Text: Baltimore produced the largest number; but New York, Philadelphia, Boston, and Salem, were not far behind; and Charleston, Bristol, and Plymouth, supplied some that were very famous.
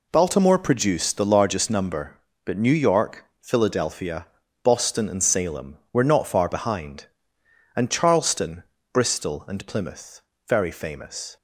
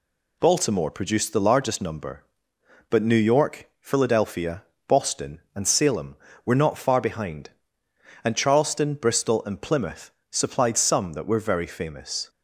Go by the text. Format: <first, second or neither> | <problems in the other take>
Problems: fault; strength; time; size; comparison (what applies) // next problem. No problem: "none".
second | skips "supplied some that were"; at 10.3 s